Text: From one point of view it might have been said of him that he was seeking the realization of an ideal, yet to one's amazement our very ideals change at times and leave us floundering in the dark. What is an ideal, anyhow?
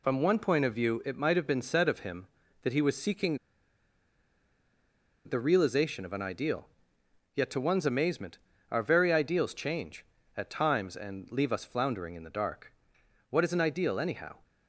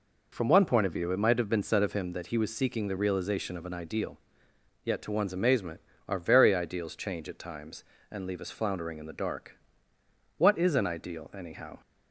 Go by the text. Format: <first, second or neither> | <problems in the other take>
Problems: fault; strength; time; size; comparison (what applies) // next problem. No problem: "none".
second | pauses between "seeking" and "the"; strong; at 3.3 s; 1.8 s long // pauses between "amazement" and "our"; slight; at 8.3 s; 0.32 s long; slight in the second